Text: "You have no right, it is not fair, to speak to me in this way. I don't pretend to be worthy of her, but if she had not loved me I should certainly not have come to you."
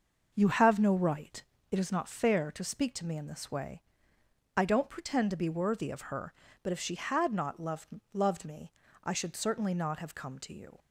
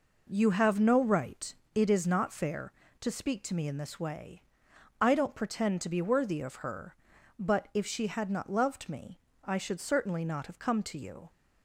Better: second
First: starts louder than the rest; noticeable; until 1.3 s; 6 dB // says "loved" twice; at 8.1 s // pauses between "me" and "I"; slight; at 8.7 s; 0.34 s long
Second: pauses between "me" and "I"; slight; at 9.1 s; 0.28 s long

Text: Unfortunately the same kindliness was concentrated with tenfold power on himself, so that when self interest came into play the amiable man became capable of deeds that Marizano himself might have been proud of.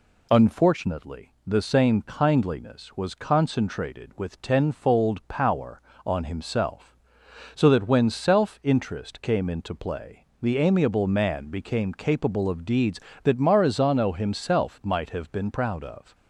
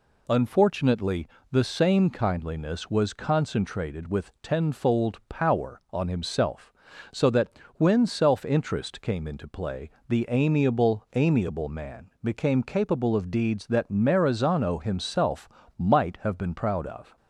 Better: first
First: pauses between "play" and "the"; slight; at 10.2 s; 0.16 s long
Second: pauses between "Unfortunately" and "the"; slight; at 1.2 s; 0.24 s long // pauses between "that" and "when"; slight; at 7.5 s; 0.26 s long // pauses between "play" and "the"; slight; at 9.9 s; 0.18 s long // says "amiable" twice; at 11.1 s // pauses between "himself" and "might"; slight; at 15.4 s; 0.28 s long

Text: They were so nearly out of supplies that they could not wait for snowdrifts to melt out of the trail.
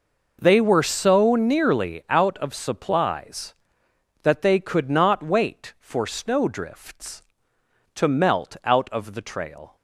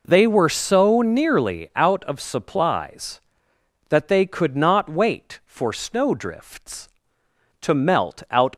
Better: first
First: none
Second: stops before "of the trail"; at 8.5 s

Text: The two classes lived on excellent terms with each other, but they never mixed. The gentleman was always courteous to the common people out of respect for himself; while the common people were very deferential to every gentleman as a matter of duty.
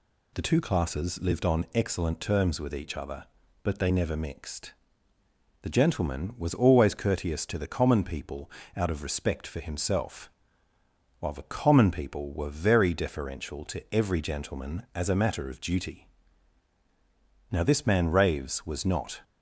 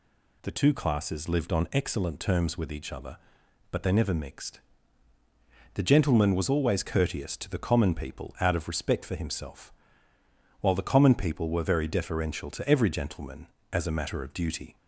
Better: second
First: pauses between "people" and "out"; slight; at 8.4 s; 0.28 s long // goes on to say "Now this man Raves was not"; strong; from 17.5 s on; 1.7 s long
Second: none

